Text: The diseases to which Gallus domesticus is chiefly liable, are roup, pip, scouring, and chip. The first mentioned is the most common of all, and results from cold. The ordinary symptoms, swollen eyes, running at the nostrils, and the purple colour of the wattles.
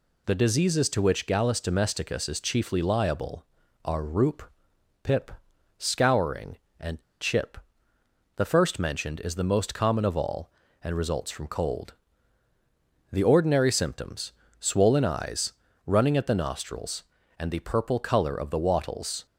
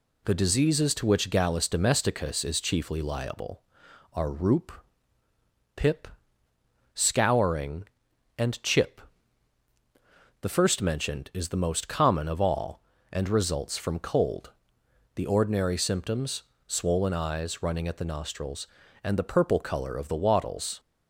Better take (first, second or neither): second